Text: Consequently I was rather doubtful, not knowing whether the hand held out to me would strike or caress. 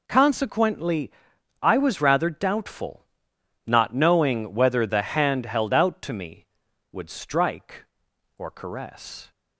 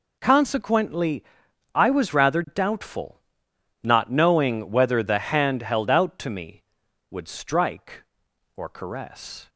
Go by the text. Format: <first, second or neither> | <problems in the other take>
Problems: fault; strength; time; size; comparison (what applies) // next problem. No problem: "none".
neither | pauses between "Consequently" and "I"; noticeable; the same in both